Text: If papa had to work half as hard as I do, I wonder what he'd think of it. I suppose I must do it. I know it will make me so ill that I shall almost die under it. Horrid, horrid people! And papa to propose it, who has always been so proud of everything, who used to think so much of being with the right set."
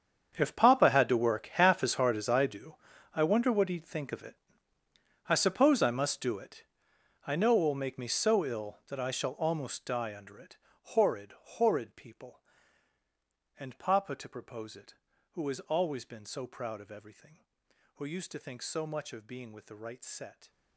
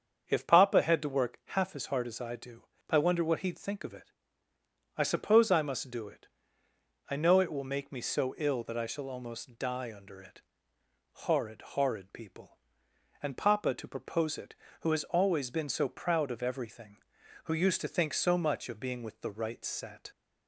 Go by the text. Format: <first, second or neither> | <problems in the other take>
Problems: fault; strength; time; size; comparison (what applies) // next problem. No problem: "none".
second | gets quieter; strong; throughout; 17.5 dB // starts louder than the rest; strong; until 1.3 s; 7.5 dB; strong in the second